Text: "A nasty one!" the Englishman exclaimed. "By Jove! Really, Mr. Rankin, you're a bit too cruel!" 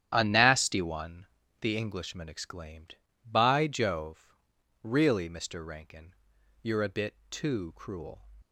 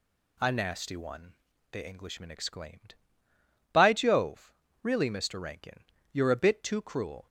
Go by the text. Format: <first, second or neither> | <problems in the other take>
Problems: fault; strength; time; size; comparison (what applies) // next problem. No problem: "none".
second | starts louder than the rest; strong; until 1.6 s; 10 dB // pauses between "bit" and "too"; slight; at 7.1 s; 0.16 s long